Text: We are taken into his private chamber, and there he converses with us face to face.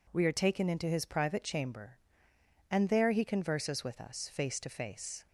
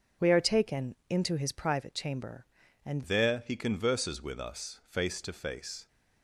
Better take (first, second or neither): first